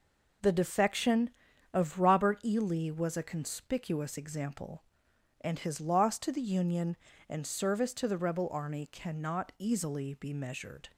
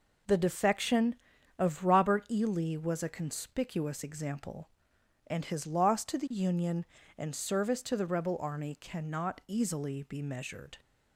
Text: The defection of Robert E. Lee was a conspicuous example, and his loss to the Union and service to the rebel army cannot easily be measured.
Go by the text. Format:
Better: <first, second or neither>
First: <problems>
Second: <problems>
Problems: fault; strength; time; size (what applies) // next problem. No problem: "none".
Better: neither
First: none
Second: none